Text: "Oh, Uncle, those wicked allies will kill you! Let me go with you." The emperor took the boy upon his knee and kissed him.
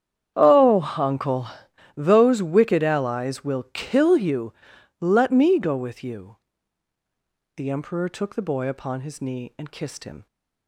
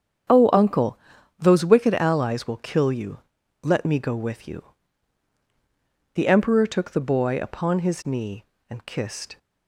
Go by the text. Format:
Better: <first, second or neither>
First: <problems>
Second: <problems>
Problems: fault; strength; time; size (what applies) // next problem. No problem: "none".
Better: first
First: starts louder than the rest; strong; until 1.3 s; 9 dB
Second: starts louder than the rest; strong; until 1.7 s; 7.5 dB // stops before "him"; at 9.3 s